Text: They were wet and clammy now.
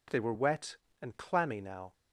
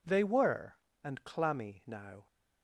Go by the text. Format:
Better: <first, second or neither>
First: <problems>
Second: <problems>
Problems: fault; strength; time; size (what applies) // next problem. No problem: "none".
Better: first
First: none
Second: skips "wet"; at 0.8 s